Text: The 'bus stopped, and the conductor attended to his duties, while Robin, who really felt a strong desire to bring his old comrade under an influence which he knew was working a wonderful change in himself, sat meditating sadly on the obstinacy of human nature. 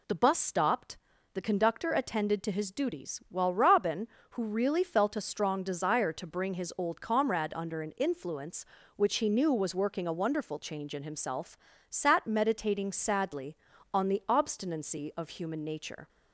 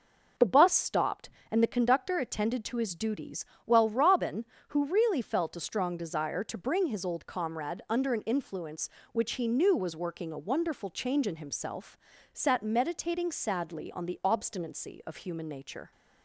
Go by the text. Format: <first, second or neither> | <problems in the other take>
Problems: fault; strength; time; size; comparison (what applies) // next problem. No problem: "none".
second | skips "and"; at 1.1 s